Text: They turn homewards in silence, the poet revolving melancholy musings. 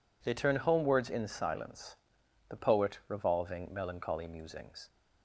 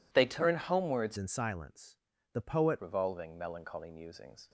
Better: first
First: none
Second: changes voice from "in" to "poet"; from 1.1 to 2.7 s; 1.6 s long

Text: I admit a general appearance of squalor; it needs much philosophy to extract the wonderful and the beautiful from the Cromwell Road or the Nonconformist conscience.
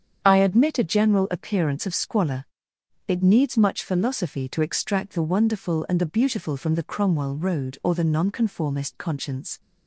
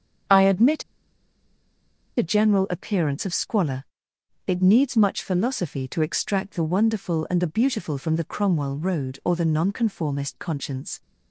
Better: first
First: starts louder than the rest; strong; until 1.2 s; 8 dB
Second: starts louder than the rest; strong; until 2.6 s; 8 dB // pauses between "admit" and "a"; strong; at 0.8 s; 1.3 s long

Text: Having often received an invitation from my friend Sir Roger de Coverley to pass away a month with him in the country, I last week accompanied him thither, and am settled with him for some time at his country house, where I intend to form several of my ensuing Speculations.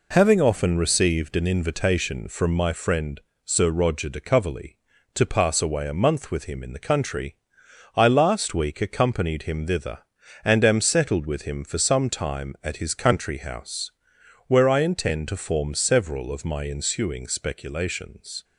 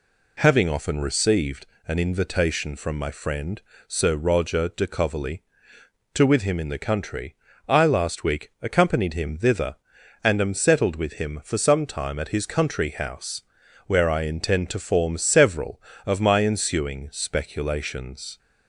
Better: first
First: pauses between "friend" and "Sir"; slight; at 3.2 s; 0.24 s long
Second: pauses between "received" and "an"; slight; at 1.6 s; 0.22 s long // pauses between "friend" and "Sir"; slight; at 3.6 s; 0.28 s long // skips "pass away a month"; at 6.2 s

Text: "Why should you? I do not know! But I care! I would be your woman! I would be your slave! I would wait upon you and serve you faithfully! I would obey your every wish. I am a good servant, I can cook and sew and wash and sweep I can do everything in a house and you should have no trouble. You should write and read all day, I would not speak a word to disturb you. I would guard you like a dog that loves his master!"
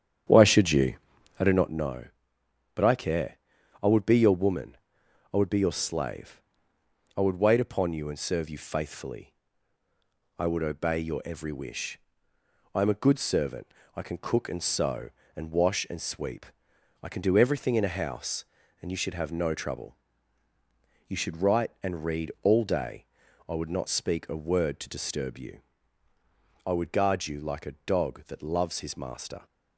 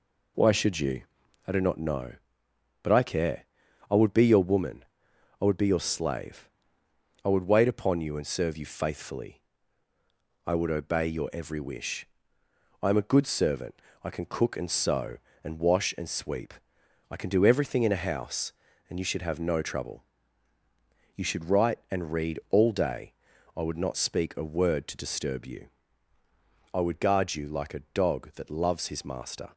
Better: second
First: starts louder than the rest; strong; until 1.8 s; 9 dB // pauses between "sweep" and "I"; noticeable; at 16.4 s; 0.56 s long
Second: pauses between "sweep" and "I"; noticeable; at 16.5 s; 0.56 s long

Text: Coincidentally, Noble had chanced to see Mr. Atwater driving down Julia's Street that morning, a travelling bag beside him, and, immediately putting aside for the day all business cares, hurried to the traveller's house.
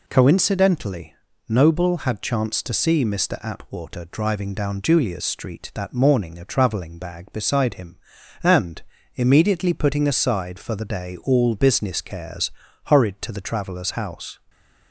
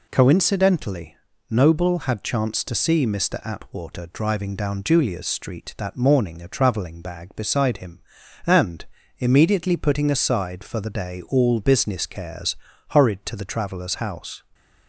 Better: neither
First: none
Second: none

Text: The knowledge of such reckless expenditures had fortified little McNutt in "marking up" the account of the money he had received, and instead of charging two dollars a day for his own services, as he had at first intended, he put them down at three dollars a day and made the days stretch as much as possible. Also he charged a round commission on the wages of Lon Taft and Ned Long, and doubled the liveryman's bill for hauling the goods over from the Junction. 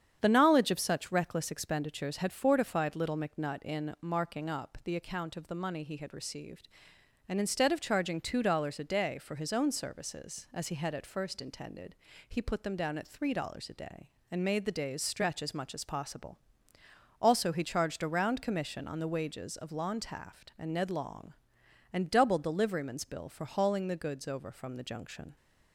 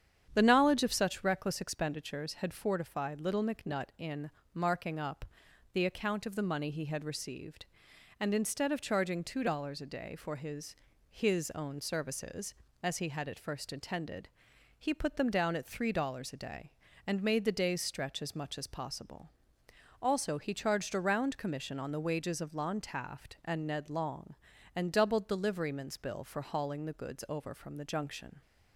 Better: first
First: starts louder than the rest; strong; until 1.2 s; 8.5 dB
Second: starts louder than the rest; strong; until 1.3 s; 8.5 dB // pauses between "in" and "marking"; slight; at 4.2 s; 0.24 s long // pauses between "up" and "the"; noticeable; at 5.2 s; 0.48 s long // says "his" twice; at 11.0 s

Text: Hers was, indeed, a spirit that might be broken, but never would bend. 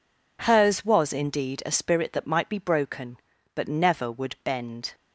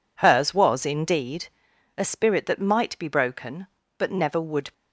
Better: first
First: none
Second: stops before "bend"; at 4.7 s

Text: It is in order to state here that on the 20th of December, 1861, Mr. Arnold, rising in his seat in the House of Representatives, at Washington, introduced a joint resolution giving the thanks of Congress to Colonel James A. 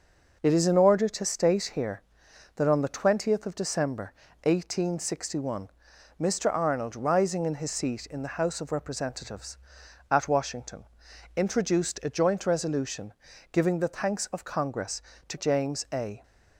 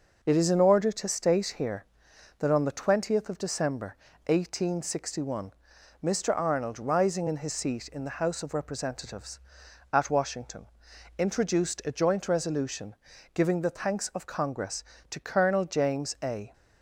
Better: second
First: pauses between "resolution" and "giving"; at 13.1 s; 0.38 s long // skips "Colonel"; at 15.3 s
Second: pauses between "resolution" and "giving"; at 12.9 s; 0.38 s long

